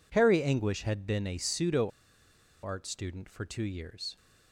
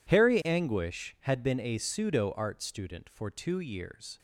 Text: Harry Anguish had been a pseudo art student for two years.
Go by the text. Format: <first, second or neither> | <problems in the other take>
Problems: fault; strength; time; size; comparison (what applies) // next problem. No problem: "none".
second | pauses between "pseudo" and "art"; noticeable; at 1.8 s; 0.75 s long